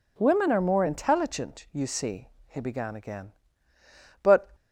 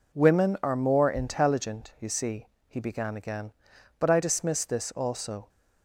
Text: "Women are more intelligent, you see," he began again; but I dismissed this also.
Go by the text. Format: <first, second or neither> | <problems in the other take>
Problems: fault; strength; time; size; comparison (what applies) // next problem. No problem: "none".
second | stops before "I dismissed this also"; at 4.5 s